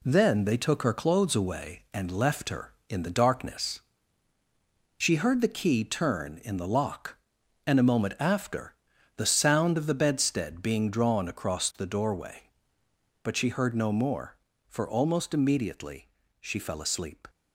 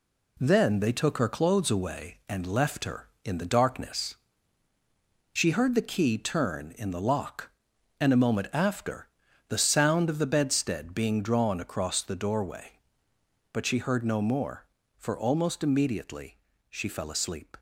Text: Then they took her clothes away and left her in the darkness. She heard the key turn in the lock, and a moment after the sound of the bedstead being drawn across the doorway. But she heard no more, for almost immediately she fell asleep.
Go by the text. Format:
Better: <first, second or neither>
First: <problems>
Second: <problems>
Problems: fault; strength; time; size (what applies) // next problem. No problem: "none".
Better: neither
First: pauses between "after" and "the"; at 8.7 s; 0.42 s long // pauses between "immediately" and "she"; slight; at 16.0 s; 0.32 s long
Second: pauses between "after" and "the"; at 9.0 s; 0.40 s long // pauses between "immediately" and "she"; slight; at 16.3 s; 0.32 s long